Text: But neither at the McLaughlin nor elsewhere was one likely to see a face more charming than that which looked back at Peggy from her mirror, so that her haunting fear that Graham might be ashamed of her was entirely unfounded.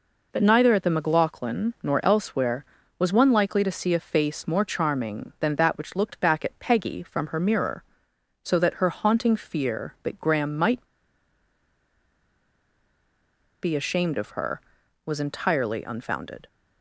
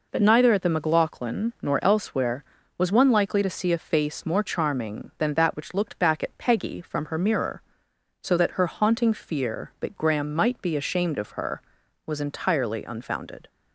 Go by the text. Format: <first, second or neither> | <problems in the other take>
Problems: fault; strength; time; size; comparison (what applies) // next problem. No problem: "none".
second | pauses between "might" and "be"; strong; at 10.8 s; 2.7 s long